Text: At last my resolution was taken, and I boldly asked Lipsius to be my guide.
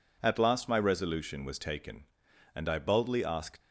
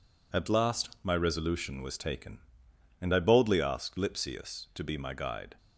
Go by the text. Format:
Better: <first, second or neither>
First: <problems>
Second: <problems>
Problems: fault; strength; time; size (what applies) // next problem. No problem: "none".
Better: second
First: stops before "Lipsius to be my guide"; at 3.6 s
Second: none